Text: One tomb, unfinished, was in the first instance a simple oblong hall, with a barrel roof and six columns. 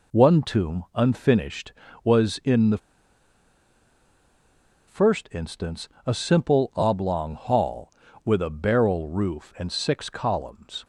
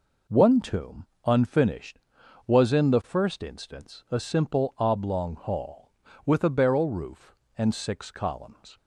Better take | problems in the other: second | pauses between "the" and "first"; strong; at 2.7 s; 2.1 s long // pauses between "instance" and "a"; slight; at 5.8 s; 0.16 s long

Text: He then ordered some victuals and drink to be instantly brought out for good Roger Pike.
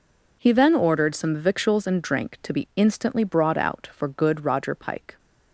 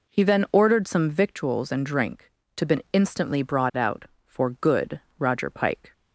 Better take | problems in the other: first | says "been" for "be"; at 2.6 s // pauses between "good" and "Roger"; slight; at 5.0 s; 0.18 s long

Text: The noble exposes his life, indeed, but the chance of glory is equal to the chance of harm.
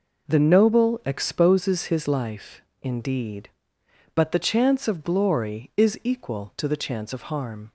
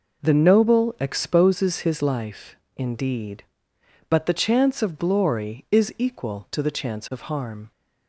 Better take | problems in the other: neither | none

